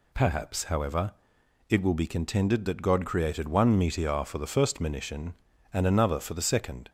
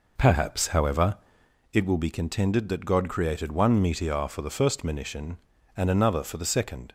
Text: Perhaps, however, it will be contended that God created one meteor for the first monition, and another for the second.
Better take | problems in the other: first | starts louder than the rest; noticeable; until 1.6 s; 4.5 dB

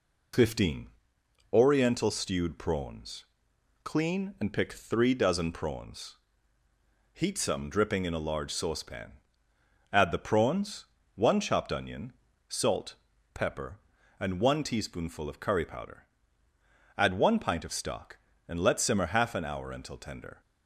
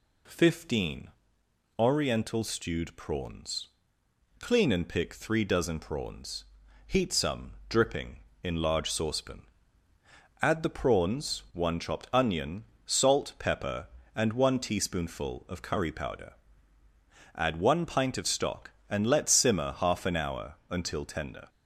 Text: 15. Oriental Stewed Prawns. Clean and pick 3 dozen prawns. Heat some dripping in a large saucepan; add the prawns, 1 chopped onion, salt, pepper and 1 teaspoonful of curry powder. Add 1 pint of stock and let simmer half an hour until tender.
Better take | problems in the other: first | pauses between "some" and "dripping"; slight; at 7.5 s; 0.18 s long // skips "a"; at 8.5 s

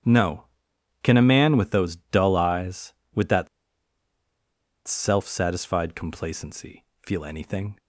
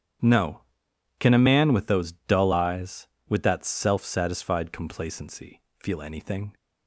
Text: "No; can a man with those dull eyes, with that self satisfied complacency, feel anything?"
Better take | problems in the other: second | starts louder than the rest; strong; until 1.6 s; 9.5 dB; strong in the second // pauses between "that" and "self"; strong; at 3.4 s; 1.3 s long

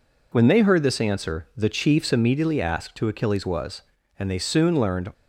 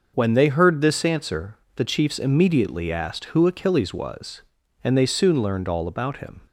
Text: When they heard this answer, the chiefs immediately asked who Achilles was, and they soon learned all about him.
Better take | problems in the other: second | stops before "all about him"; at 5.1 s

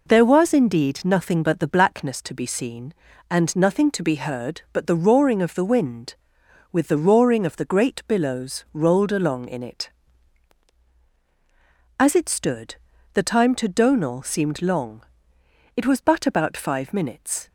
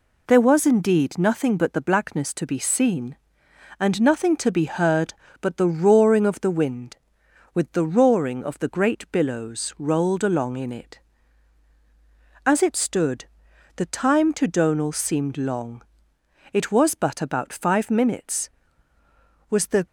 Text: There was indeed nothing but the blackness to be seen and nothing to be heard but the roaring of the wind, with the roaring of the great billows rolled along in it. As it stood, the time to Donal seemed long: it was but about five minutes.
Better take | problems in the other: first | goes on to say "Was the"; slight; from 19.4 s on; 0.36 s long

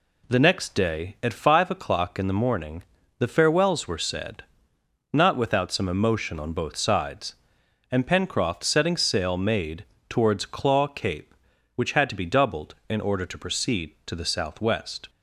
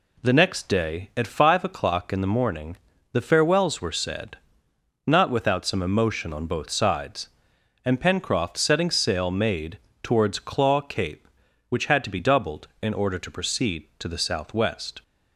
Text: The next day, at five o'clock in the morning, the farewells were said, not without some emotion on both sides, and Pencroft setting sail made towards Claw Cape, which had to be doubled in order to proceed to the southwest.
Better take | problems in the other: neither | pauses between "made" and "towards"; slight; the same in both

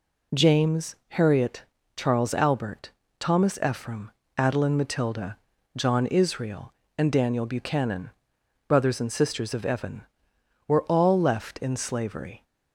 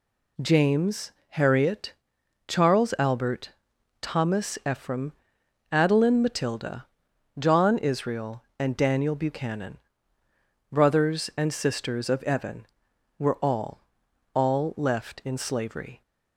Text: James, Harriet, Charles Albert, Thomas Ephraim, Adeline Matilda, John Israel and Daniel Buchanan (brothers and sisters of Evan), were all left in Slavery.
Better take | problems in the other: first | says "all" twice; at 14.3 s

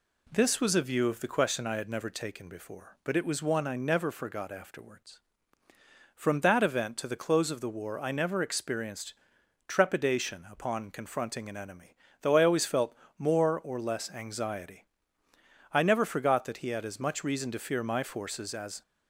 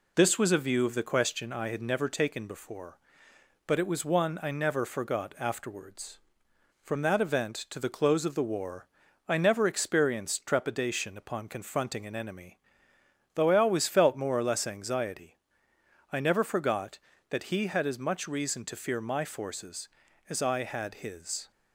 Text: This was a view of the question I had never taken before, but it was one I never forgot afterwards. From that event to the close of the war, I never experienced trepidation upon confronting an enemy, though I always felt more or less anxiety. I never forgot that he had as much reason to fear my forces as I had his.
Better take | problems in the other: second | pauses between "experienced" and "trepidation"; noticeable; at 9.1 s; 0.54 s long // pauses between "felt" and "more"; slight; at 12.9 s; 0.24 s long // stops before "I had his"; at 18.8 s

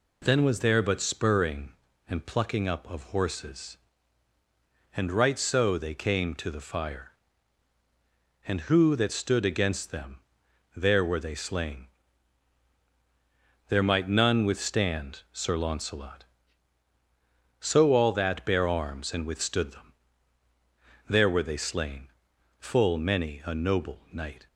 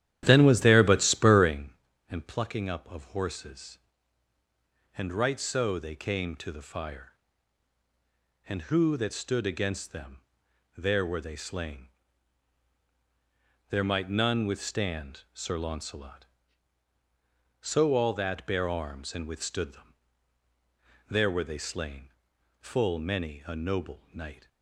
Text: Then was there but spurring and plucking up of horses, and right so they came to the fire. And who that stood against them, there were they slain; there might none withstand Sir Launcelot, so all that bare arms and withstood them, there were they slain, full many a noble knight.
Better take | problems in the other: first | starts louder than the rest; strong; until 1.7 s; 11.5 dB

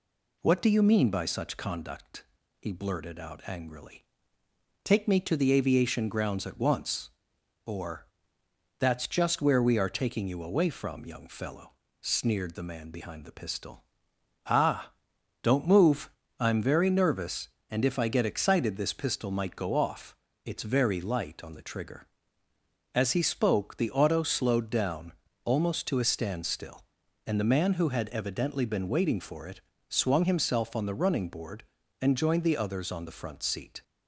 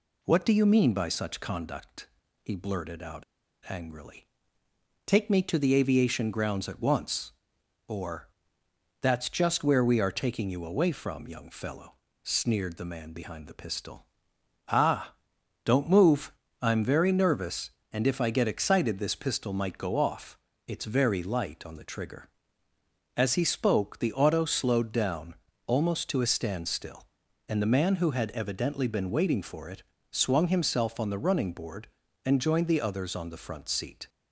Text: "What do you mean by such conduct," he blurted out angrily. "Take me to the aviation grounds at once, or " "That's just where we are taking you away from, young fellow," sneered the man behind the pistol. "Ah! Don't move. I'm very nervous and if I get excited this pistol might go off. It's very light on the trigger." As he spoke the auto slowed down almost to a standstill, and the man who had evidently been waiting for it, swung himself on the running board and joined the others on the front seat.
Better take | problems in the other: first | pauses between "out" and "angrily"; at 3.2 s; 0.44 s long // pauses between "down" and "almost"; slight; at 25.3 s; 0.30 s long; slight in the first

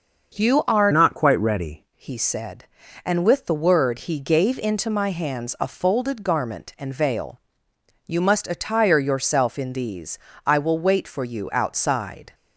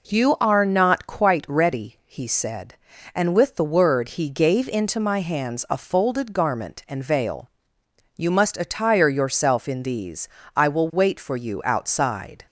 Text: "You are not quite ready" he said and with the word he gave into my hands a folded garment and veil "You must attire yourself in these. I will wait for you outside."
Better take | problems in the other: second | starts louder than the rest; noticeable; until 1.4 s; 6 dB // changes voice from "not" to "ready"; from 0.9 to 1.8 s; 0.9 s long // pauses between "veil" and "You"; noticeable; at 7.3 s; 0.66 s long; noticeable in the second

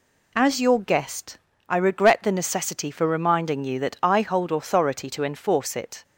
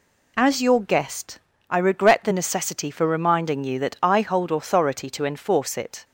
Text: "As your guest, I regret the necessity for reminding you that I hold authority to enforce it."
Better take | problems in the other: neither | none

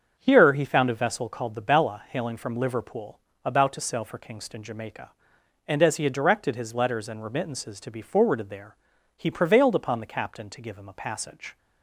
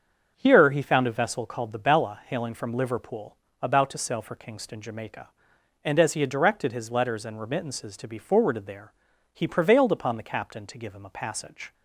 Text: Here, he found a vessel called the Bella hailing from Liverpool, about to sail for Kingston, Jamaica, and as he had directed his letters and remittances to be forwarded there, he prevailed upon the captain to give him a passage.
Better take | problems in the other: neither | starts louder than the rest; the same in both

